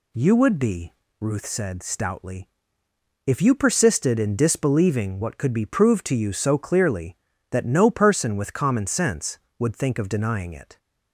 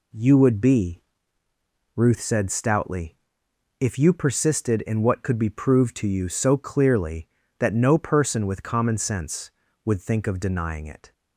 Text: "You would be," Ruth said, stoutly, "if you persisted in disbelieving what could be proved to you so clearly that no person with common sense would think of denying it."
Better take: first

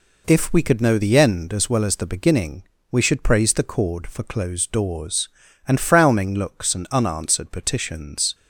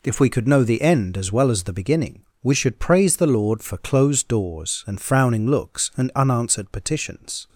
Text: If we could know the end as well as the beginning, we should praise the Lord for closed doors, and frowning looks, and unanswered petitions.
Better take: second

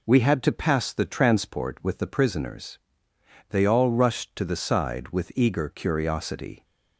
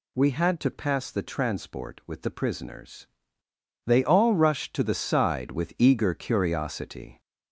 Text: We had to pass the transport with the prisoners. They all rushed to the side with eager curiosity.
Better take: first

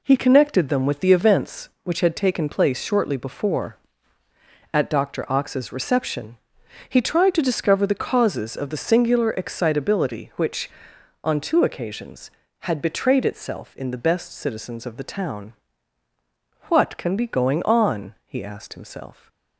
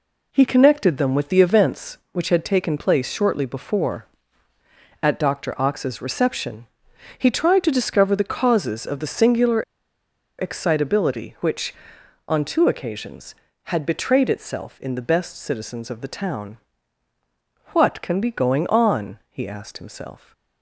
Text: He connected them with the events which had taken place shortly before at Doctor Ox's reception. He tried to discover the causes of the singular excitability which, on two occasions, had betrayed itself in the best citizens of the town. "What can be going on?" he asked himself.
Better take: first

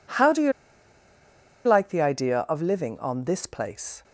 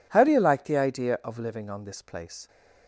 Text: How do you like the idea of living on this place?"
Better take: second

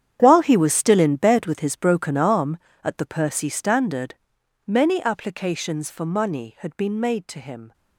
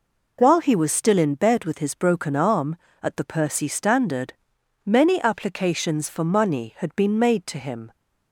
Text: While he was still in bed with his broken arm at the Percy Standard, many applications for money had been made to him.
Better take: second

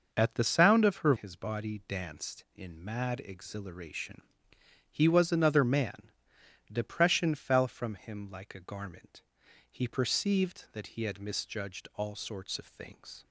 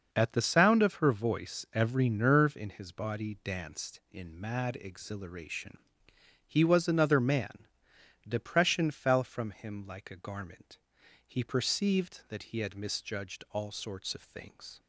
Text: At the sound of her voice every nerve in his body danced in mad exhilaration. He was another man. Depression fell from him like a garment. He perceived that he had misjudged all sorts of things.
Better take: second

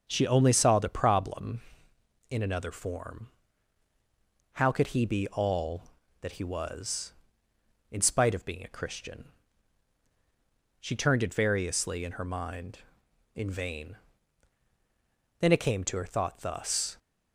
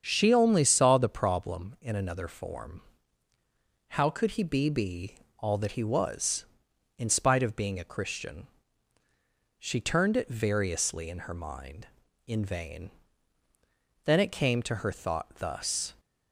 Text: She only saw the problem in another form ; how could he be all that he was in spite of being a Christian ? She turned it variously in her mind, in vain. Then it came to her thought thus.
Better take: first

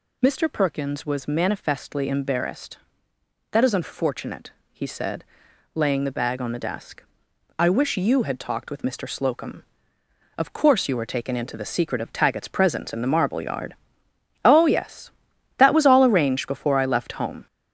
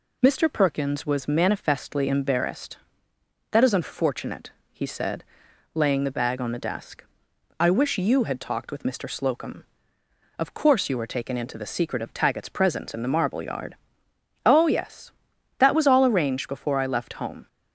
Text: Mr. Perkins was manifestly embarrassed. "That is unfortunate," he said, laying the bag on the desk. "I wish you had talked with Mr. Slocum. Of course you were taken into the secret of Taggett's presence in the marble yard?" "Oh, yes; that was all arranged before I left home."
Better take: second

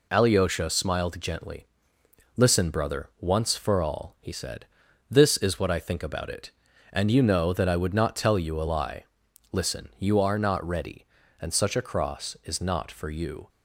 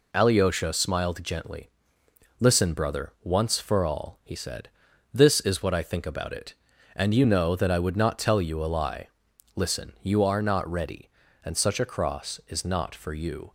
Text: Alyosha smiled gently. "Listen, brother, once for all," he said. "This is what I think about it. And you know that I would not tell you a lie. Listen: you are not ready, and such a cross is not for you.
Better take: neither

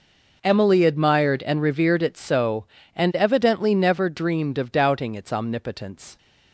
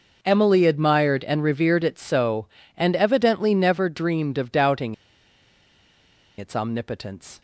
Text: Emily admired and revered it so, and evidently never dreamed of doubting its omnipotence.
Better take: first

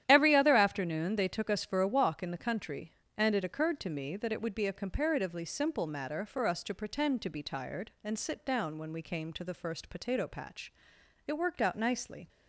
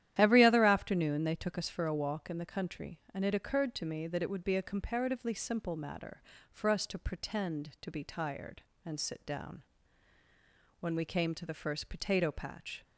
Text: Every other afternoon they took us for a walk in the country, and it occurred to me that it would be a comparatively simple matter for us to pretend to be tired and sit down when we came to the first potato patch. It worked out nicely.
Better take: first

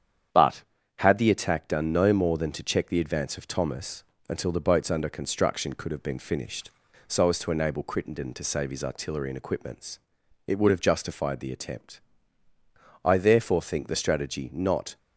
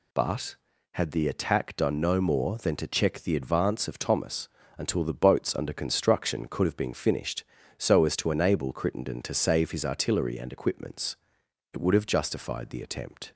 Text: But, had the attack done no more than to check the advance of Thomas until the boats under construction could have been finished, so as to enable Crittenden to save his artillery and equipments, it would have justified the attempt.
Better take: second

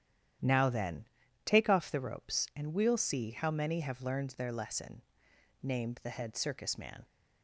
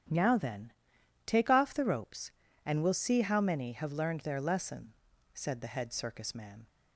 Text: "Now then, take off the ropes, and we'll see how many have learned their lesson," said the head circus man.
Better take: second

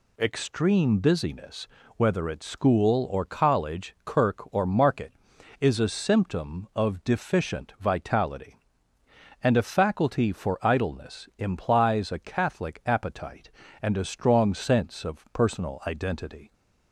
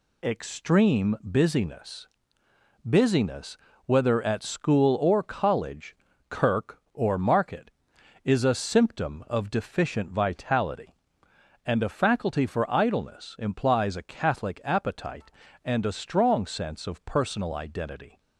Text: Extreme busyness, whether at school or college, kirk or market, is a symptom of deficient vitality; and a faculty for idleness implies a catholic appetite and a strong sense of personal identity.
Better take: first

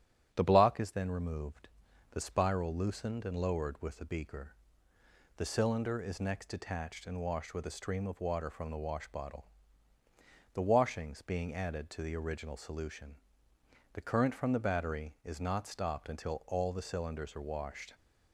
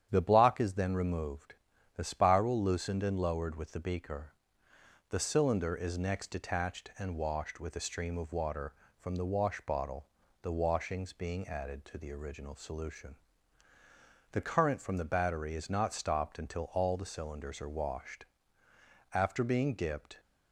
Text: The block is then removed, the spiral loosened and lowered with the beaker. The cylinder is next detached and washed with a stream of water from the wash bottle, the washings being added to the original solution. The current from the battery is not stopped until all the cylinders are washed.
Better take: first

